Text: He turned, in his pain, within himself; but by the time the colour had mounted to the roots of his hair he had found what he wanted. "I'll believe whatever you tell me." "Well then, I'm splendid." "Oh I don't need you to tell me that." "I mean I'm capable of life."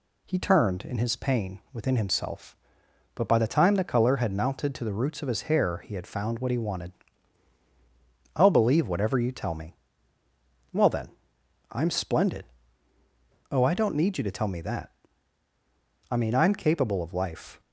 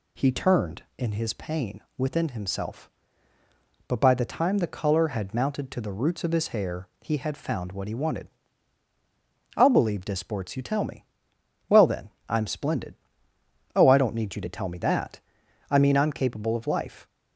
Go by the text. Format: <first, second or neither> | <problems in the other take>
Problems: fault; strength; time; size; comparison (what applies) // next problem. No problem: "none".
first | pauses between "hair" and "he"; slight; at 6.8 s; 0.16 s long // says "disports" for "whatever"; at 10.0 s